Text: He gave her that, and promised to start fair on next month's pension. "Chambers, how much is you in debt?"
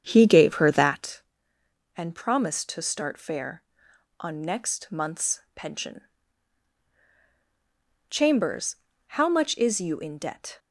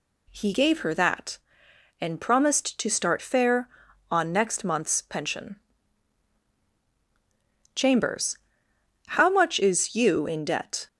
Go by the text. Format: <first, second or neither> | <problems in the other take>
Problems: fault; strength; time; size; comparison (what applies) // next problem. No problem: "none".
second | starts louder than the rest; strong; until 1.0 s; 8 dB